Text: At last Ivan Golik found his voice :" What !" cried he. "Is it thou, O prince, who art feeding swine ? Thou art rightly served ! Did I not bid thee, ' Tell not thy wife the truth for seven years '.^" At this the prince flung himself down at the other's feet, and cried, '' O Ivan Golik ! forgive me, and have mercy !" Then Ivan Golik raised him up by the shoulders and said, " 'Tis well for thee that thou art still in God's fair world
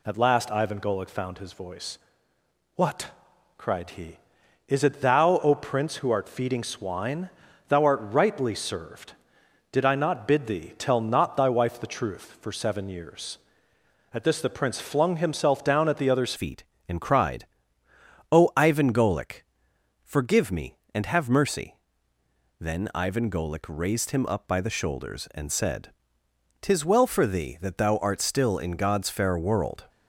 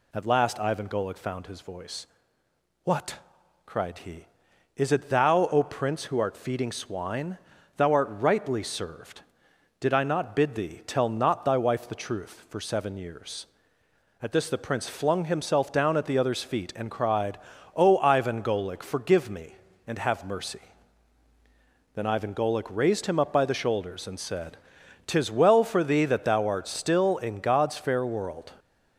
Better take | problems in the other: second | changes voice at "feet"; from 16.3 s on; 13.5 s long

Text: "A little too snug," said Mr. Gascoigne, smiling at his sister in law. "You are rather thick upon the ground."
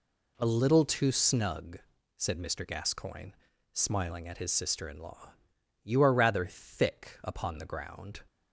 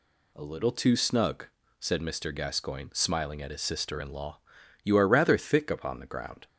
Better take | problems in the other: second | changes voice at "little"; from 0.4 s on; 7.8 s long

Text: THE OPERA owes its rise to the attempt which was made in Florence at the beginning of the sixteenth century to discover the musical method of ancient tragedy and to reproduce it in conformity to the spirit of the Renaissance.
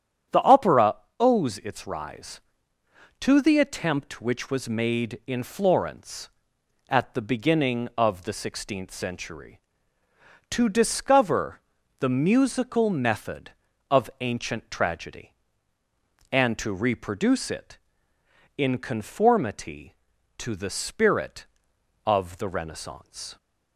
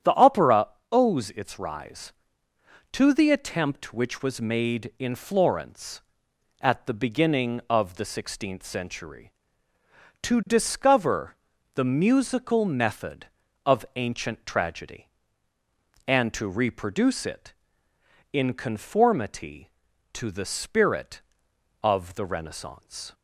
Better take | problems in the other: neither | starts louder than the rest; strong; the same in both // pauses between "OPERA" and "owes"; slight; the same in both // pauses between "discover" and "the"; the same in both

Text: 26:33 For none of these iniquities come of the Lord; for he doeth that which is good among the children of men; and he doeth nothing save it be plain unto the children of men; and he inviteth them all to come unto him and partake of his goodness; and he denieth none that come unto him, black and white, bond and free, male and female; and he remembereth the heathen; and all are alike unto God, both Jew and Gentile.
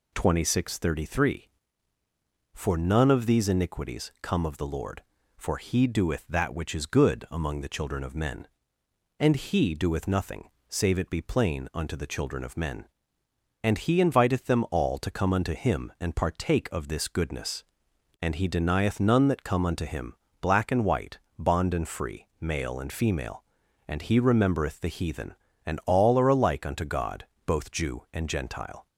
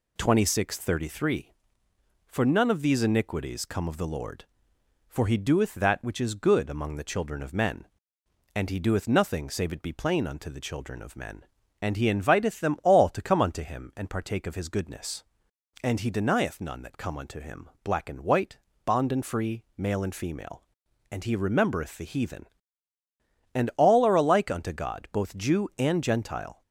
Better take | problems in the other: second | pauses between "nothing" and "save"; slight; at 10.4 s; 0.20 s long // says "this" for "his"; at 16.8 s

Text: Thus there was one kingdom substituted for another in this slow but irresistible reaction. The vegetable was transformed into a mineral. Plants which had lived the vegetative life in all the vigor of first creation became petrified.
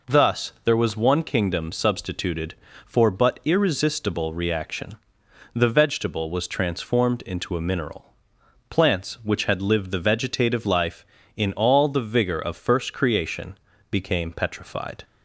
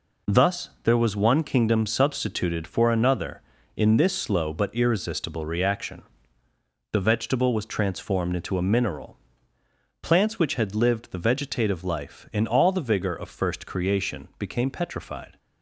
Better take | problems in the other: second | skips "another in this slow"; at 3.0 s // pauses between "creation" and "became"; slight; at 13.5 s; 0.34 s long

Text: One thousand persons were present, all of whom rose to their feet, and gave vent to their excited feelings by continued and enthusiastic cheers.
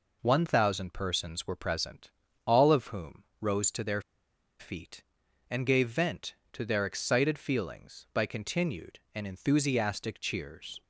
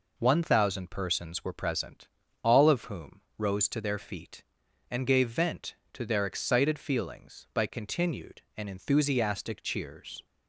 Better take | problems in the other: second | pauses between "whom" and "rose"; slight; at 3.2 s; 0.16 s long; slight in the second // pauses between "their" and "feet"; noticeable; at 4.0 s; 0.58 s long

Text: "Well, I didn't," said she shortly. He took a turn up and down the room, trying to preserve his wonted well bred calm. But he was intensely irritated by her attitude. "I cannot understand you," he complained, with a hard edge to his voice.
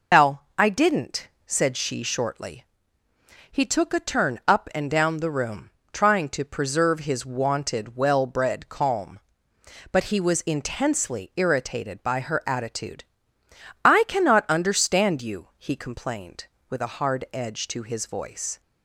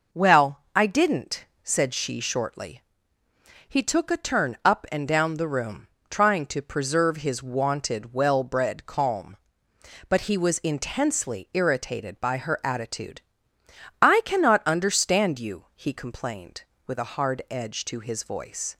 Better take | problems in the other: second | loses the start of "Well"; at 0.1 s; 160 ms

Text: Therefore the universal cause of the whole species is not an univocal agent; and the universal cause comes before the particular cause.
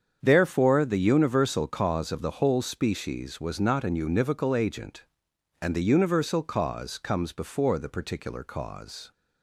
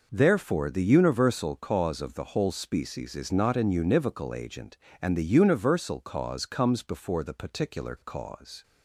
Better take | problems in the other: second | starts louder than the rest; strong; until 1.2 s; 7.5 dB // says "was" for "is"; at 3.3 s

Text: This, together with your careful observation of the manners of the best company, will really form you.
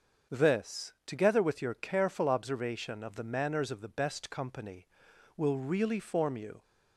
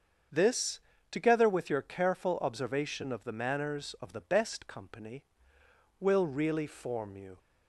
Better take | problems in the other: neither | starts louder than the rest; the same in both

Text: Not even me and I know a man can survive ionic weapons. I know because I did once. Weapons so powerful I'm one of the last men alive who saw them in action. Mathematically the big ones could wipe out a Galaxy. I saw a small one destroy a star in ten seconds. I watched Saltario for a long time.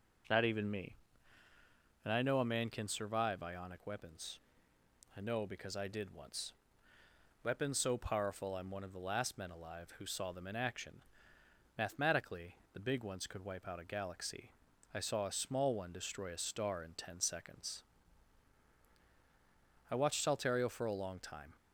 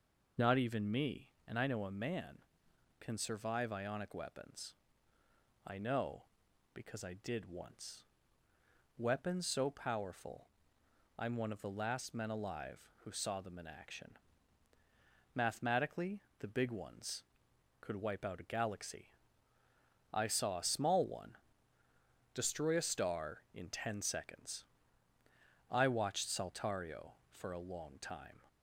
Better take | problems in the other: first | loses the start of "Not"; at 0.3 s; 25 ms // pauses between "powerful" and "I'm"; noticeable; at 10.4 s; 0.70 s long // pauses between "Mathematically" and "the"; slight; at 16.1 s; 0.20 s long; slight in the first // pauses between "one" and "destroy"; noticeable; at 21.3 s; 0.96 s long

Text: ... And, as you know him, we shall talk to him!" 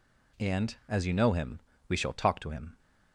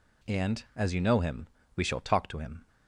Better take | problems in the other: neither | none

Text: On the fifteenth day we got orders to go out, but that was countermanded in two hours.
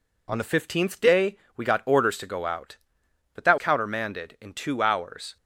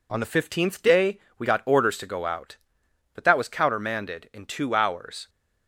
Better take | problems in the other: second | pauses between "day" and "we"; slight; at 1.3 s; 0.18 s long; slight in the second // skips "was"; at 3.5 s

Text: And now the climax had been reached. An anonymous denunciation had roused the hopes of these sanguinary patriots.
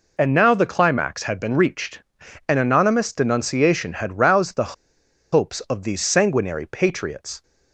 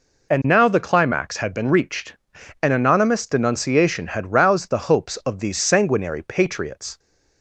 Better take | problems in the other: second | pauses between "the" and "hopes"; noticeable; at 4.7 s; 0.59 s long

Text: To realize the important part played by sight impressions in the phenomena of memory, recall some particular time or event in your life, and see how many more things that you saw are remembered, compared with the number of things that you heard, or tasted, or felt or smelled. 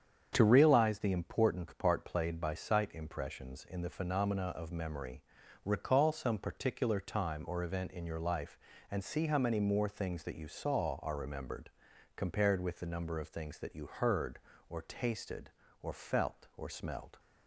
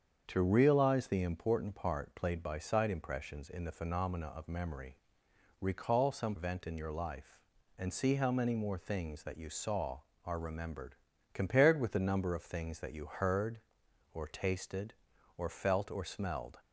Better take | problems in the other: first | starts louder than the rest; strong; until 1.2 s; 7 dB; strong in the first // skips "particular time or"; at 6.3 s

